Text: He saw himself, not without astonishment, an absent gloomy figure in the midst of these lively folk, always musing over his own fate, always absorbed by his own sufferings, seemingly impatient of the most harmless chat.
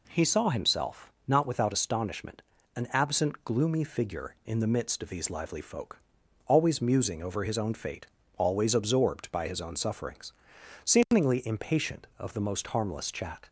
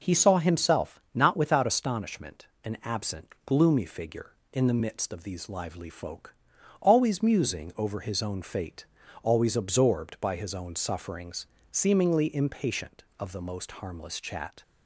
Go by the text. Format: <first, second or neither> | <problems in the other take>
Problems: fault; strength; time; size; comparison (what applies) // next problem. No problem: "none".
neither | none